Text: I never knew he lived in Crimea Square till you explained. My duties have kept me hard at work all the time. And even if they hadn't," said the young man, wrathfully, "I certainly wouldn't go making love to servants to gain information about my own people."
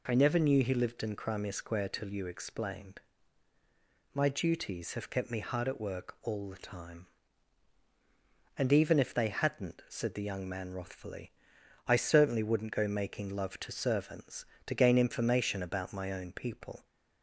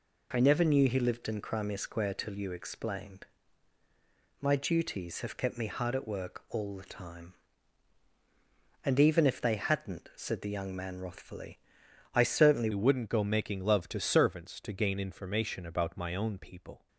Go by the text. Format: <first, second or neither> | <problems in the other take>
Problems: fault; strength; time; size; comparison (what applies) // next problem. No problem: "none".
first | changes voice at "wouldn't"; from 12.7 s on; 4.1 s long